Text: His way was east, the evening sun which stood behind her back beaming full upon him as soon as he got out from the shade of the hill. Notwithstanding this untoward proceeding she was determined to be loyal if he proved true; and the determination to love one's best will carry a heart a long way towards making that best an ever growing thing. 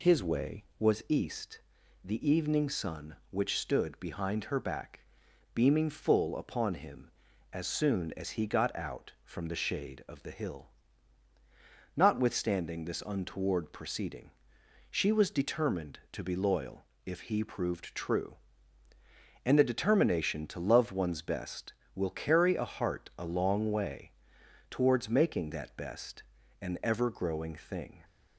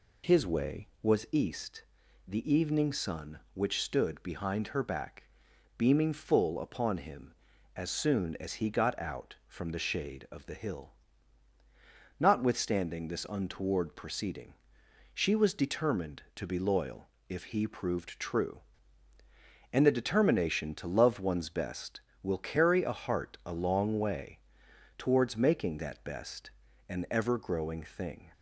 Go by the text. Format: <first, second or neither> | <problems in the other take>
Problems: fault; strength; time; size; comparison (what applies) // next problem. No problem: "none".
neither | pauses between "back" and "beaming"; noticeable; the same in both // pauses between "proceeding" and "she"; noticeable; the same in both // pauses between "loyal" and "if"; slight; the same in both // pauses between "way" and "towards"; noticeable; the same in both // pauses between "best" and "an"; slight; the same in both